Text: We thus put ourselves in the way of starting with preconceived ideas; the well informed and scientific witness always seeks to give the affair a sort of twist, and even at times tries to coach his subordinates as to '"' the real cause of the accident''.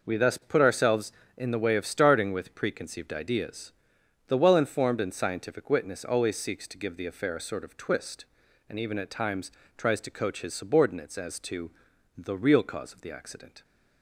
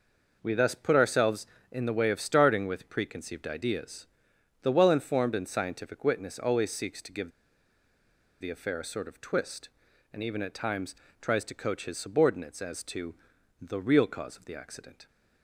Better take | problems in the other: first | pauses between "give" and "the"; at 7.2 s; 1.1 s long // pauses between "times" and "tries"; slight; at 10.9 s; 0.26 s long; slight in the first

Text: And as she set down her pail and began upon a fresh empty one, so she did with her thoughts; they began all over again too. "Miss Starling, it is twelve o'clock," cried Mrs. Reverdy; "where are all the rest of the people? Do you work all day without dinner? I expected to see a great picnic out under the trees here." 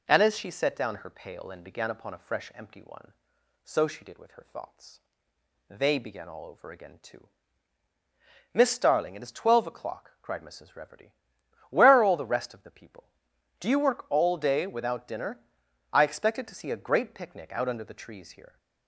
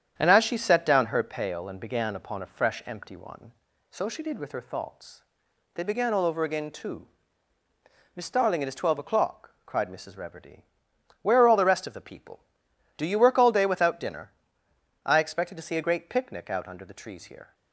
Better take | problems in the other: first | gets quieter; noticeable; throughout; 4.5 dB

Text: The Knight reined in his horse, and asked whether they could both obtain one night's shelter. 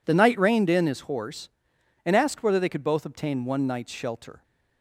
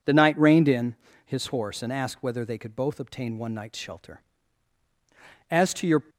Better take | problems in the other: first | pauses between "in" and "his"; slight; at 0.9 s; 0.28 s long // goes on to say "As to your"; from 5.5 s on; 0.52 s long

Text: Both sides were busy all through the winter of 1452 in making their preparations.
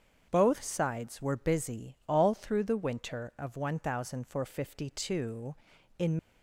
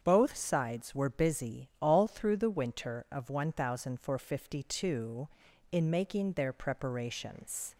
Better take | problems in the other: second | starts louder than the rest; strong; until 1.3 s; 7.5 dB; strong in the second // stops before "making their preparations"; at 6.1 s

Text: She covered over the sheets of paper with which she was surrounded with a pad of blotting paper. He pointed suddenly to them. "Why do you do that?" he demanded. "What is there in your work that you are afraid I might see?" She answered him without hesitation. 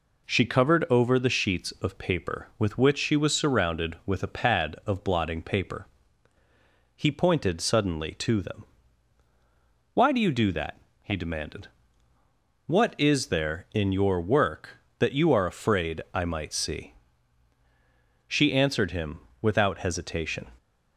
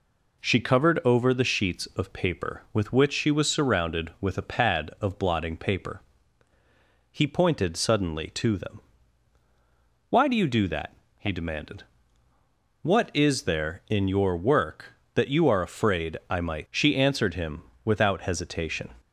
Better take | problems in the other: first | skips "see"; at 16.6 s // pauses between "him" and "without"; slight; at 17.6 s; 0.22 s long; slight in the first

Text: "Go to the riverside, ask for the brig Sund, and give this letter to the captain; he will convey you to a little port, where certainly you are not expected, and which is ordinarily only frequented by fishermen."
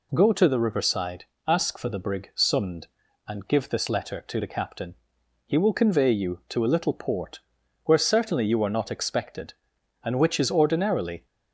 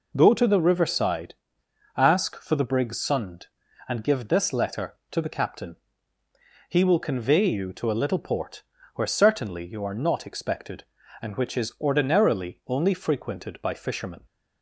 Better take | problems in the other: second | stops before "only frequented by fishermen"; at 11.2 s

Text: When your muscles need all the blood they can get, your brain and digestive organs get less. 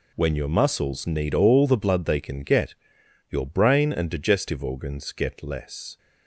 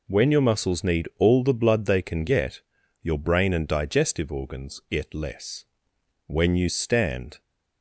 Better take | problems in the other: first | goes on to say "When you stand"; noticeable; from 6.2 s on; 1.1 s long

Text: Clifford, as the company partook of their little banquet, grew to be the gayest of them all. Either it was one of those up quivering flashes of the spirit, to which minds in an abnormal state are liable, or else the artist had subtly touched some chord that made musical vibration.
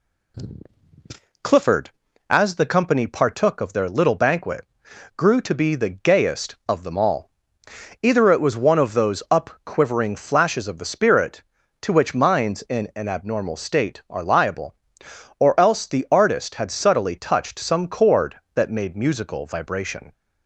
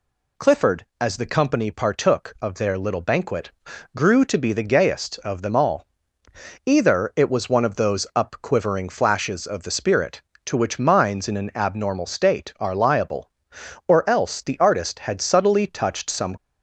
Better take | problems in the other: first | stops before "chord that made musical vibration"; at 16.3 s

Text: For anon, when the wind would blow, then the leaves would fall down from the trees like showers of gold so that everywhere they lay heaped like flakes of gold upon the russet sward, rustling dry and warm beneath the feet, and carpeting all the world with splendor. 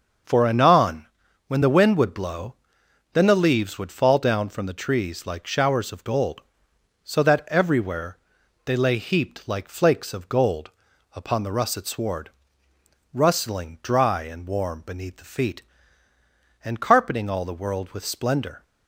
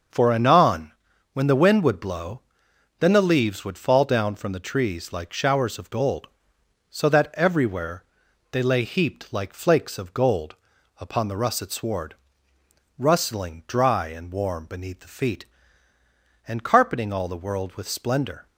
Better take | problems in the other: neither | starts louder than the rest; the same in both // pauses between "everywhere" and "they"; noticeable; the same in both // pauses between "gold" and "upon"; the same in both

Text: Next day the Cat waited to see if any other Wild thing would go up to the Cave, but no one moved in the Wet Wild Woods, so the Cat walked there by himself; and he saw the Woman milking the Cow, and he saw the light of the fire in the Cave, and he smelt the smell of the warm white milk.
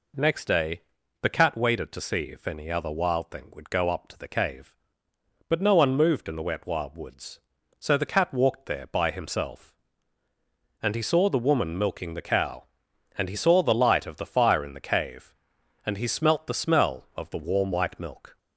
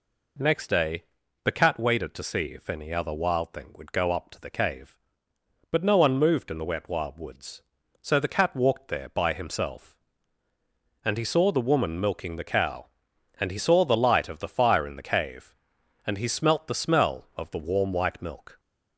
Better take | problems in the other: neither | pauses between "day" and "the"; the same in both

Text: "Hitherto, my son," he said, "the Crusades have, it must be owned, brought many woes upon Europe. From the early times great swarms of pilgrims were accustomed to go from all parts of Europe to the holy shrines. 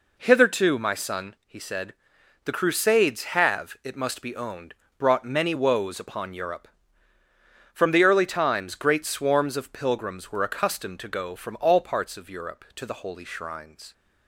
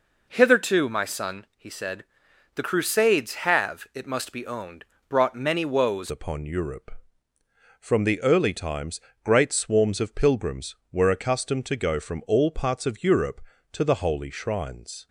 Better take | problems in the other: first | changes voice at "upon"; from 6.0 s on; 9.0 s long // pauses between "times" and "great"; slight; at 9.0 s; 0.22 s long

